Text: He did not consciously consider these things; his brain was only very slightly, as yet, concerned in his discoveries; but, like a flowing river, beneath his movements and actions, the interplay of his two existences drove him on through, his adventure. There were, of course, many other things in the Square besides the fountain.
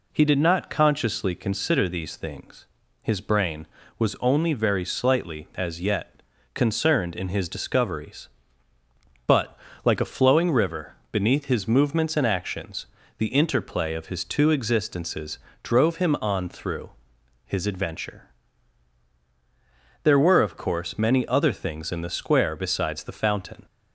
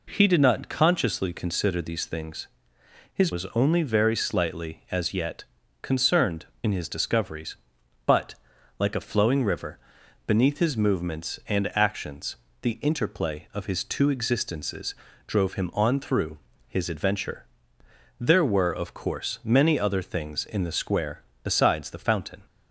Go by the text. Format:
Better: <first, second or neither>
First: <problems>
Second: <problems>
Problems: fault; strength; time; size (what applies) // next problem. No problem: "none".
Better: first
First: pauses between "existences" and "drove"; slight; at 15.3 s; 0.24 s long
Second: skips "brain"; at 3.3 s // pauses between "existences" and "drove"; slight; at 14.9 s; 0.32 s long // pauses between "Square" and "besides"; slight; at 21.2 s; 0.20 s long